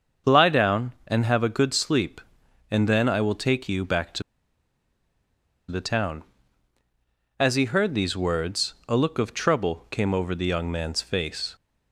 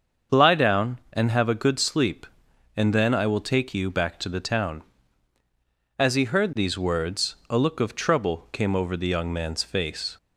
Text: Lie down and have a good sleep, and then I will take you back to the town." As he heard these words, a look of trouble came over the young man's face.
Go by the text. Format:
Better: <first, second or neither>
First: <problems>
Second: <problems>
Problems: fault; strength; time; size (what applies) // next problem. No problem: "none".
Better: second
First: starts louder than the rest; until 1.4 s; 7 dB // pauses between "to" and "the"; strong; at 4.2 s; 1.4 s long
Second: starts louder than the rest; until 1.4 s; 7 dB